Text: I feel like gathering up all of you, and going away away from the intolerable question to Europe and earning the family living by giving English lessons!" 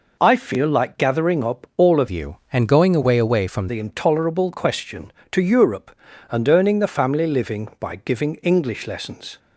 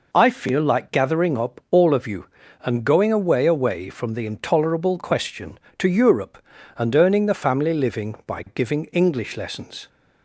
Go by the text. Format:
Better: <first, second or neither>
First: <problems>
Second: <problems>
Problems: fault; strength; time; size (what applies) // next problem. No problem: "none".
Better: second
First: changes voice from "you" to "from"; from 2.0 to 3.6 s; 1.6 s long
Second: none